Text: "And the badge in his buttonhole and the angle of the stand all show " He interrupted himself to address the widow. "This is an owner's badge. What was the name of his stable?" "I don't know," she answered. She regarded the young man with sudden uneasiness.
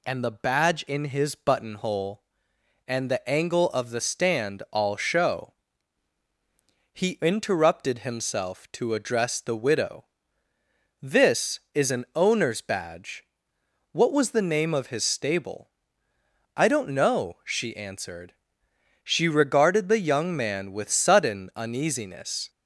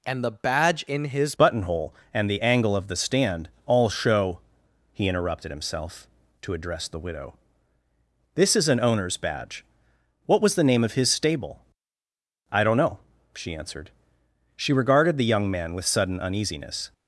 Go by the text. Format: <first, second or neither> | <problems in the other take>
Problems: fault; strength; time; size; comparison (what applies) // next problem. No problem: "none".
first | changes voice at "buttonhole"; from 1.3 s on; 15.6 s long // pauses between "stand" and "all"; slight; at 3.4 s; 0.18 s long